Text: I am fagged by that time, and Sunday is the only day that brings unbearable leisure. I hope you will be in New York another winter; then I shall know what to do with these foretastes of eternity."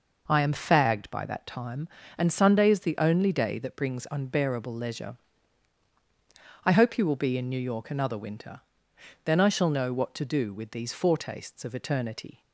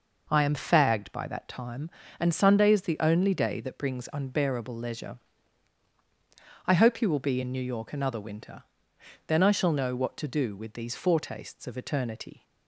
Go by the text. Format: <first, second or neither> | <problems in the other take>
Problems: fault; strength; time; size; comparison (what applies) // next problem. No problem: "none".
neither | none